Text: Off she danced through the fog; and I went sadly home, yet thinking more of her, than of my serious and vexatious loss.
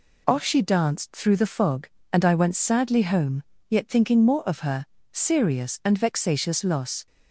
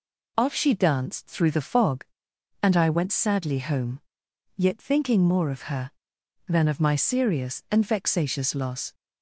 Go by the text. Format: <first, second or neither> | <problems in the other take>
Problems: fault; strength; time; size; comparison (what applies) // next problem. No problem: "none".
second | skips "than of my"; at 4.9 s